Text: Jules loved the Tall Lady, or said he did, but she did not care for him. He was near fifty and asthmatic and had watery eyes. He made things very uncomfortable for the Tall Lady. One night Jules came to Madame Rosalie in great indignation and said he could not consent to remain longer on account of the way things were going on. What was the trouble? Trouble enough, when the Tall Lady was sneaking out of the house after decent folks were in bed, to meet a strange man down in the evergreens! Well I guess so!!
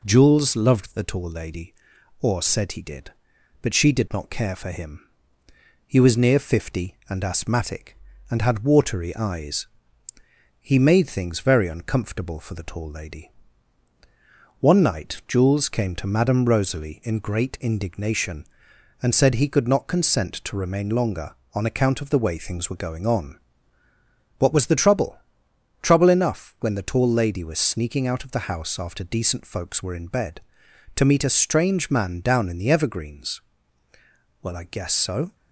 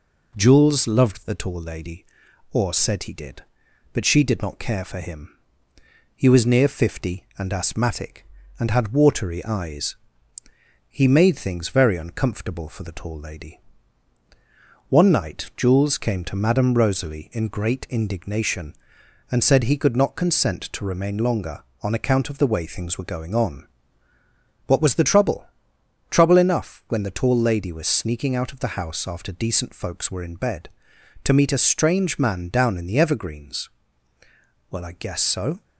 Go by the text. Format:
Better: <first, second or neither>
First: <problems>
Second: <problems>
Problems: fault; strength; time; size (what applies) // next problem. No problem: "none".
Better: neither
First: none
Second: none